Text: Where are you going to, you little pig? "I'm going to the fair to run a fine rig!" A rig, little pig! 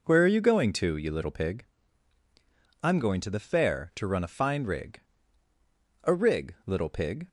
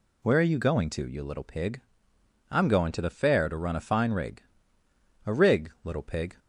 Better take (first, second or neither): neither